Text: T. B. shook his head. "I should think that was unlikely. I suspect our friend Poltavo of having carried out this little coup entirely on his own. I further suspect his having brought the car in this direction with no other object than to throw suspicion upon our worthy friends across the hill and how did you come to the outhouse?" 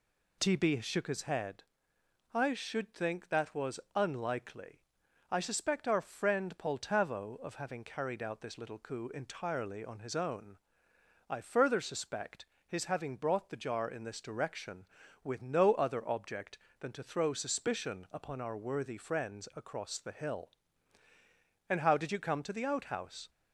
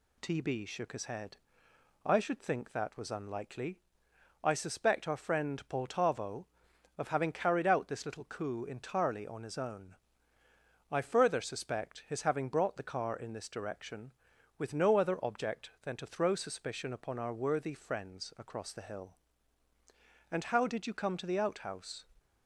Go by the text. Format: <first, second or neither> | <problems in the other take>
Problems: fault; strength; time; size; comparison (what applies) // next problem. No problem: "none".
second | pauses between "was" and "unlikely"; slight; at 3.8 s; 0.16 s long // pauses between "suspect" and "his"; slight; at 12.4 s; 0.22 s long // says "jar" for "car"; at 13.5 s